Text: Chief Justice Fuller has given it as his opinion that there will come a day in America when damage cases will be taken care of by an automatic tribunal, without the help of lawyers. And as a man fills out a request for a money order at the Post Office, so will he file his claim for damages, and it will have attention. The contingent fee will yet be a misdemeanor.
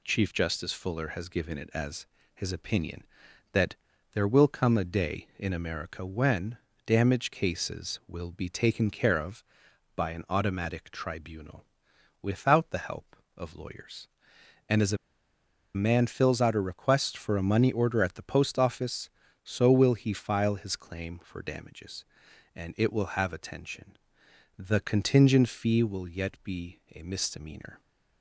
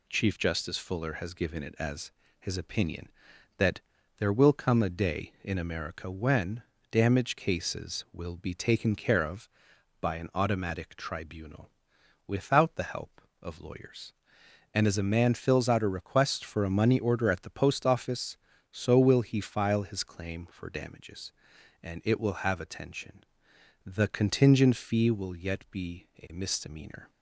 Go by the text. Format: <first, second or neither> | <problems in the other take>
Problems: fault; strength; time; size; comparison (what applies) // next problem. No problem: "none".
second | pauses between "as" and "his"; slight; at 2.0 s; 0.28 s long; slight in the second // pauses between "that" and "there"; at 3.7 s; 0.38 s long; also in the second // pauses between "when" and "damage"; slight; at 6.5 s; 0.28 s long; slight in the second // pauses between "a" and "man"; noticeable; at 14.9 s; 0.78 s long